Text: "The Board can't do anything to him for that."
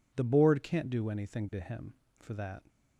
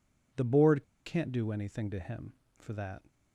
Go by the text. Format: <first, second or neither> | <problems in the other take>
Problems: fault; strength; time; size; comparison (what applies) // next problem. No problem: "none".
first | pauses between "Board" and "can't"; slight; at 0.8 s; 0.23 s long